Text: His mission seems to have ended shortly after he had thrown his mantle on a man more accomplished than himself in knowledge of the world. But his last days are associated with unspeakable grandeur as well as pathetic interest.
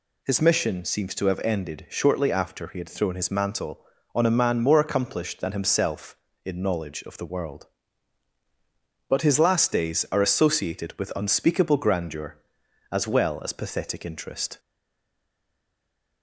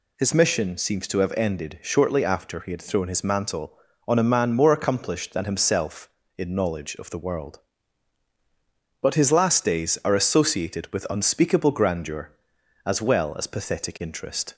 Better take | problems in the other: second | stays silent after the last word; noticeable; from 14.5 s on; 1.7 s long

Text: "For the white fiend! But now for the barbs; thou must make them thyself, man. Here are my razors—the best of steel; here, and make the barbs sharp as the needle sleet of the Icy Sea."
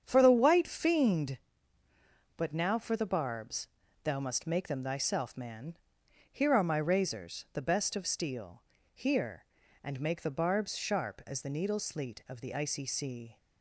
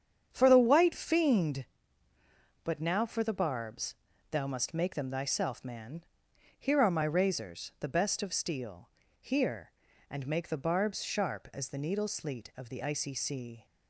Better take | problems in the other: neither | starts louder than the rest; strong; the same in both

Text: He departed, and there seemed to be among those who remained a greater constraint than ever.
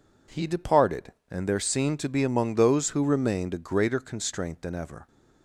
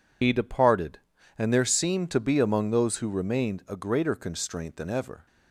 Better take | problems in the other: first | loses the start of "He"; at 0.2 s; 70 ms

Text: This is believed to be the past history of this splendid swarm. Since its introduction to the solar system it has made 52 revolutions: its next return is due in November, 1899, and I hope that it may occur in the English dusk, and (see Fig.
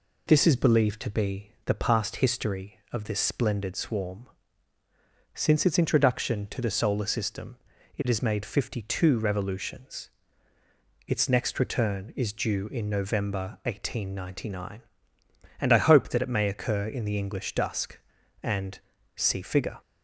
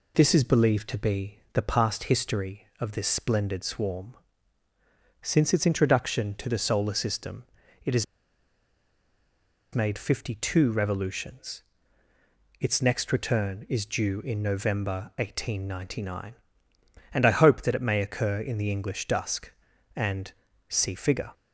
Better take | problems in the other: first | pauses between "system" and "it"; at 7.4 s; 0.40 s long; also in the first // pauses between "has" and "made"; strong; at 8.0 s; 1.7 s long

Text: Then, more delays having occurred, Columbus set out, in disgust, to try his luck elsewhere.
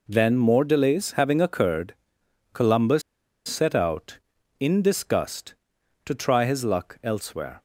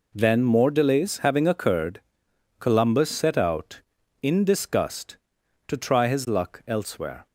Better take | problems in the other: second | pauses between "Columbus" and "set"; noticeable; at 3.0 s; 0.46 s long

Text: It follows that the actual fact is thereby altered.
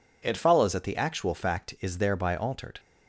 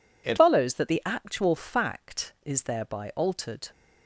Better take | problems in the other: first | changes voice at "follows"; from 0.3 s on; 3.4 s long

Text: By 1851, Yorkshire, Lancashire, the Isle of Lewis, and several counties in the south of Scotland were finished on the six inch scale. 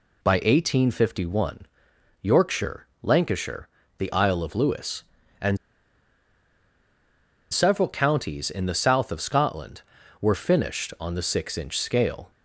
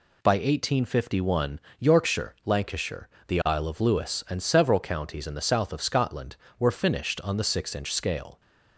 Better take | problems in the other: second | pauses between "and" and "several"; strong; at 5.5 s; 1.9 s long

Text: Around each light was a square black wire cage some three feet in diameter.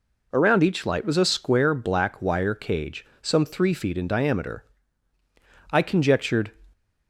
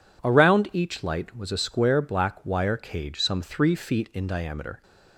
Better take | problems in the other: second | pauses between "cage" and "some"; slight; at 3.0 s; 0.16 s long // goes on to say "I conjectured"; noticeable; from 5.7 s on; 0.80 s long

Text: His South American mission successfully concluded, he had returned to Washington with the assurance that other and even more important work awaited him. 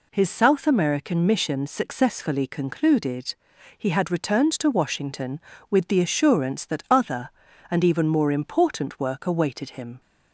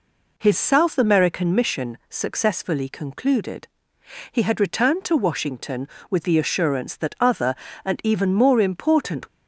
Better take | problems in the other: first | stops before "work awaited him"; at 9.2 s

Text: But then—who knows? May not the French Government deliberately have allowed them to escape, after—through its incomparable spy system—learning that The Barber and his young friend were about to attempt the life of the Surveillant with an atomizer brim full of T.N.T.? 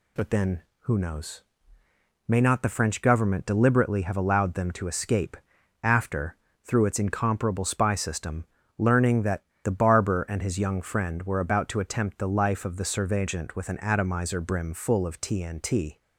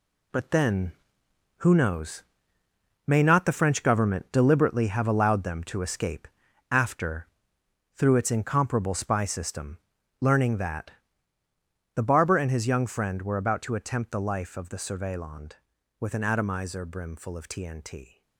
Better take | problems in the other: first | gets quieter; strong; throughout; 8.5 dB // pauses between "that" and "The"; at 10.9 s; 1.0 s long; slight in the first

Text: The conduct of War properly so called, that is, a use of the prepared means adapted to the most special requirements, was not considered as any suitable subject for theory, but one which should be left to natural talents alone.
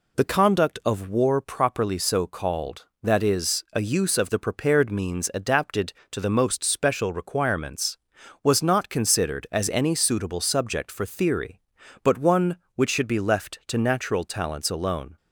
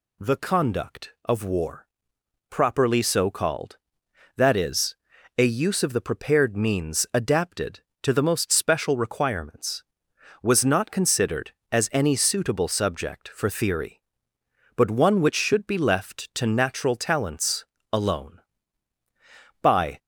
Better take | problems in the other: first | pauses between "War" and "properly"; noticeable; at 1.8 s; 0.64 s long // pauses between "talents" and "alone"; slight; at 17.6 s; 0.28 s long // goes on to say "By"; slight; from 19.6 s on; 0.36 s long

